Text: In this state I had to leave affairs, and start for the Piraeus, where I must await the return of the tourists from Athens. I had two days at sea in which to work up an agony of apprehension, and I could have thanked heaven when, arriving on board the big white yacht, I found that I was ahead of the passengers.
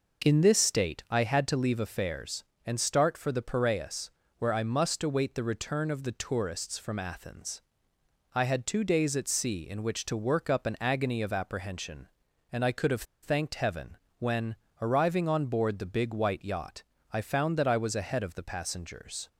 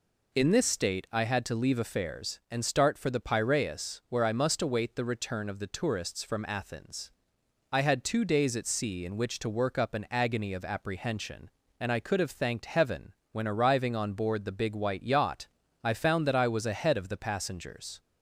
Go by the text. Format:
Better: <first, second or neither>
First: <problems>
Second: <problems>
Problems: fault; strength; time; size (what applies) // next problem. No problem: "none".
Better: second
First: pauses between "have" and "thanked"; slight; at 13.0 s; 0.20 s long // pauses between "heaven" and "when"; slight; at 13.9 s; 0.20 s long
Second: pauses between "heaven" and "when"; slight; at 13.1 s; 0.20 s long